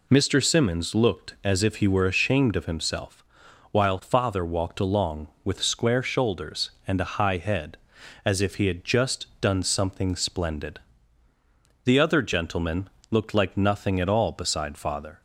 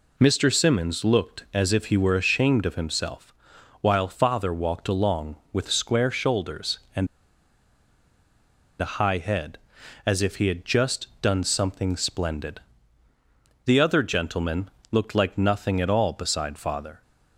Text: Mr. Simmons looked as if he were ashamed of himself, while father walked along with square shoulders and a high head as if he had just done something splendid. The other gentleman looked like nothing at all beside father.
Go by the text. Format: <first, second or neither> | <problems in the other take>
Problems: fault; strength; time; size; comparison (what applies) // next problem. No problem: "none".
first | pauses between "and" and "a"; strong; at 7.0 s; 1.7 s long // pauses between "gentleman" and "looked"; slight; at 14.6 s; 0.22 s long; slight in the first